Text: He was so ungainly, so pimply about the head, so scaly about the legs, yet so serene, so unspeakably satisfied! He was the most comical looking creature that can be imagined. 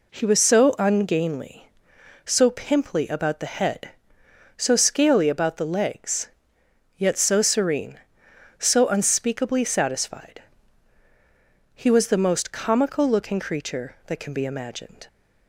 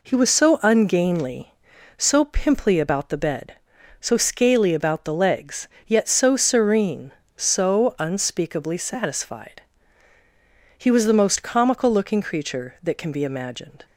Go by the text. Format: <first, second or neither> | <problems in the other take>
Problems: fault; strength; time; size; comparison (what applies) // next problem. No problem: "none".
first | says "bed" for "head"; at 3.1 s